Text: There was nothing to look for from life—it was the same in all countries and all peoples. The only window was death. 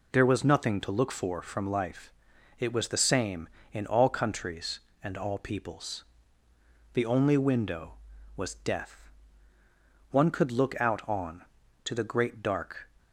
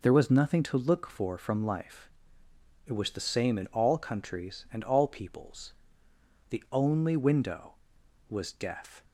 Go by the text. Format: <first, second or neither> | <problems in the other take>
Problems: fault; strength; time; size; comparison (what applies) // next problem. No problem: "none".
second | goes on to say "One could look out on to the great dark"; strong; from 10.1 s on; 2.8 s long